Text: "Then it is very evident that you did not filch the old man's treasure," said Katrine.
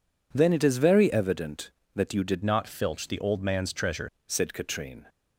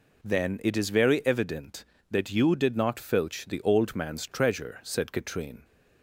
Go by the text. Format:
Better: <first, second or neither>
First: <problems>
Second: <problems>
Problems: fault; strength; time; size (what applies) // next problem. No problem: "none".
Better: second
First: changes voice from "not" to "treasure"; from 2.4 to 4.0 s; 1.6 s long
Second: none